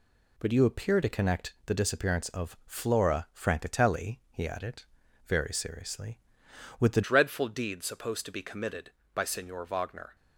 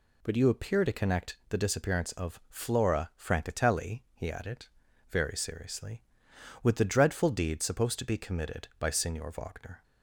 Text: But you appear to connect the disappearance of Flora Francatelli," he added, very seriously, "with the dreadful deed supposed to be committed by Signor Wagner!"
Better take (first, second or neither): second